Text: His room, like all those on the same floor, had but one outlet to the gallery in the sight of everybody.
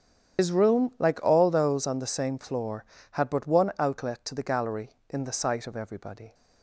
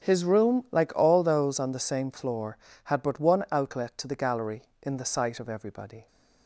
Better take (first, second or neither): second